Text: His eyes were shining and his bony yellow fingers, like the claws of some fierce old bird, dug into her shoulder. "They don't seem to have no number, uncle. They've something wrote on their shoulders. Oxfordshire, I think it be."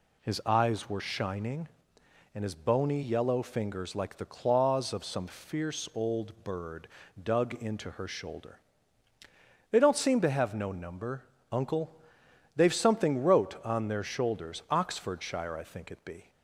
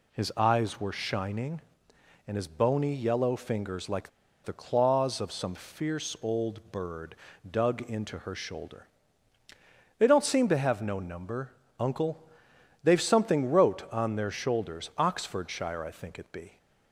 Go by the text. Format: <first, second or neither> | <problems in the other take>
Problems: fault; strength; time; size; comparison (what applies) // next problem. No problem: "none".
first | pauses between "like" and "the"; slight; at 4.0 s; 0.35 s long